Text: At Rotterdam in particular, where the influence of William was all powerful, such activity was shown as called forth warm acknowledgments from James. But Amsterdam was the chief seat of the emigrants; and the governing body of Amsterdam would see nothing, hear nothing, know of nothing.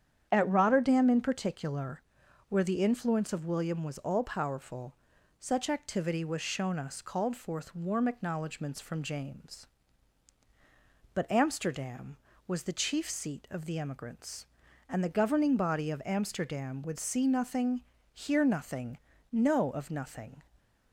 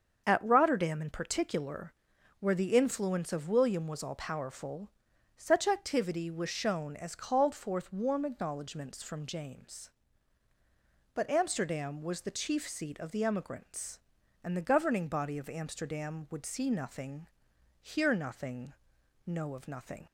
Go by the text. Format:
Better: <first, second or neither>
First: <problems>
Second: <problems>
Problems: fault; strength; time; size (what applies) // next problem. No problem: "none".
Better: second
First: starts louder than the rest; strong; until 1.3 s; 9 dB // says "us" for "as"; at 6.7 s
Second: starts louder than the rest; until 1.2 s; 7 dB